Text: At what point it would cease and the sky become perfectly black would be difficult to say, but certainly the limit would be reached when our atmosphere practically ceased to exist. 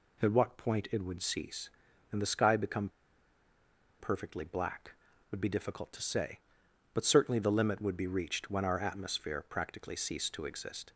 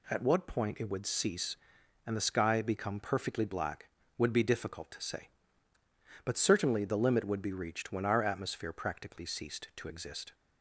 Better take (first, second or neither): second